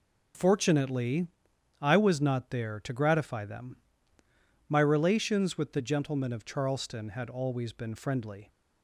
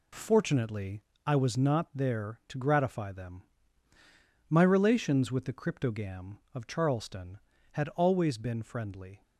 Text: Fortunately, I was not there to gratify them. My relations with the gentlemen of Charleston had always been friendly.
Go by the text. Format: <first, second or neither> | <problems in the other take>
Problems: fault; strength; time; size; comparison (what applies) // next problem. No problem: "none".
first | says "cryptogam" for "gentlemen"; at 5.5 s